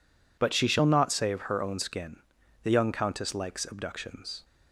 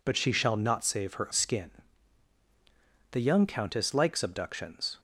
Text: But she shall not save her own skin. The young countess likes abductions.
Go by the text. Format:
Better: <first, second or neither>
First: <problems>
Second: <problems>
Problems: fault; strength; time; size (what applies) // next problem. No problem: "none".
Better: first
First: none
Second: skips "own"; at 1.3 s